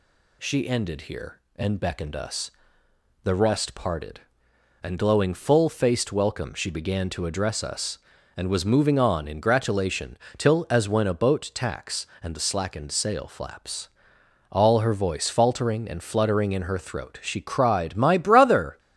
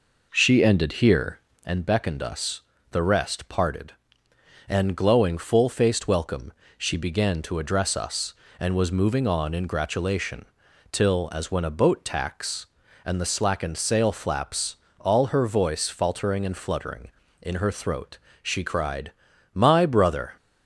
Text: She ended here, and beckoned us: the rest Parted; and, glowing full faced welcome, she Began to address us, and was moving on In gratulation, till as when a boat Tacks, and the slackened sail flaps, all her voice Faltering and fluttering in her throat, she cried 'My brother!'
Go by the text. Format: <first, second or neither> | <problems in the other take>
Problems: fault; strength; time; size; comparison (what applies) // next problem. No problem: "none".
first | starts louder than the rest; noticeable; until 1.8 s; 4.5 dB // pauses between "cried" and "My"; noticeable; at 19.0 s; 0.46 s long